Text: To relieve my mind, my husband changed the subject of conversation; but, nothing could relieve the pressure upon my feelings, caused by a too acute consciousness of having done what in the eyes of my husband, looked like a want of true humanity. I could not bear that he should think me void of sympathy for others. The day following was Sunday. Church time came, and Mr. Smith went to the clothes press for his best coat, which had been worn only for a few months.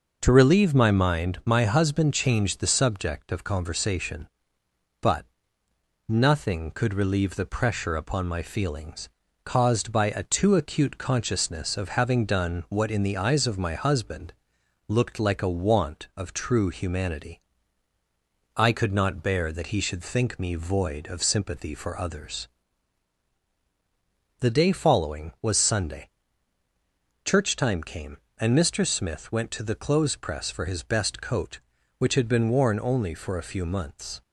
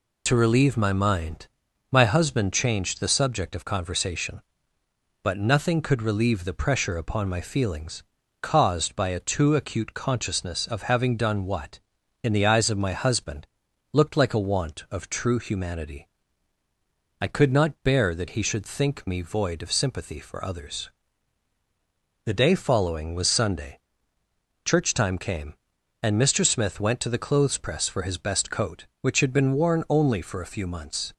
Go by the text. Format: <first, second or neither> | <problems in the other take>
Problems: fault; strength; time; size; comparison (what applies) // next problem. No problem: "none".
first | loses the start of "To"; at 0.2 s; 40 ms